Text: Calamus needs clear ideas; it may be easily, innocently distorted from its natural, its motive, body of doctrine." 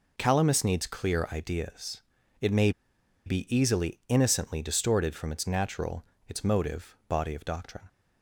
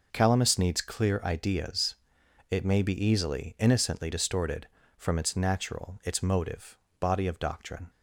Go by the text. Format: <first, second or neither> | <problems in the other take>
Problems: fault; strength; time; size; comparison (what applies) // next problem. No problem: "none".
second | pauses between "may" and "be"; noticeable; at 2.7 s; 0.55 s long